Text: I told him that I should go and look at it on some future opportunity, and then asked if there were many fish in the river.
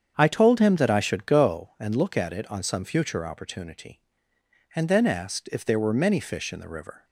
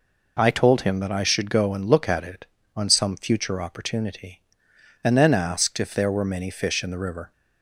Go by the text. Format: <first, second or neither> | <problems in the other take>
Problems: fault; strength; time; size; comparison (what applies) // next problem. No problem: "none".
second | starts louder than the rest; strong; until 1.6 s; 7.5 dB